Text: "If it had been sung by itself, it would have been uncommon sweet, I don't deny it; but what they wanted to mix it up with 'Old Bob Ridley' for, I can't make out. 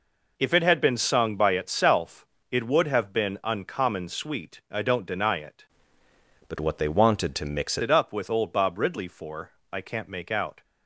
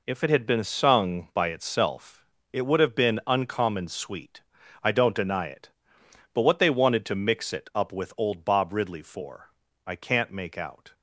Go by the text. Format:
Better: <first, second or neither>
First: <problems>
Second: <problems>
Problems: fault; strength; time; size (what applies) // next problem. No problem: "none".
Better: second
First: changes voice from "but" to "mix"; from 6.4 to 7.7 s; 1.3 s long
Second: none